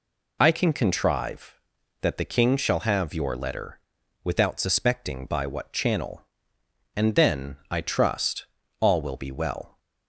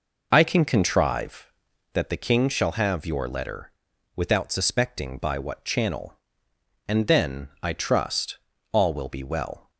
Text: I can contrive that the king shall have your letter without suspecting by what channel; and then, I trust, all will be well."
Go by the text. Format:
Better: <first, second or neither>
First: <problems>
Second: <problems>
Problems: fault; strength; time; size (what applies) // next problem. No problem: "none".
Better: first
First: pauses between "letter" and "without"; noticeable; at 3.7 s; 0.46 s long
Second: starts louder than the rest; noticeable; until 2.0 s; 5 dB // pauses between "letter" and "without"; noticeable; at 3.7 s; 0.46 s long